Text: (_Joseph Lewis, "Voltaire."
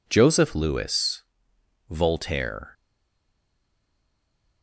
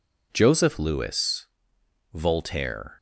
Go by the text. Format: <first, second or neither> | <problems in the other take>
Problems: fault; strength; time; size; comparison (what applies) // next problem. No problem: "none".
second | stays silent after the last word; noticeable; from 2.7 s on; 1.9 s long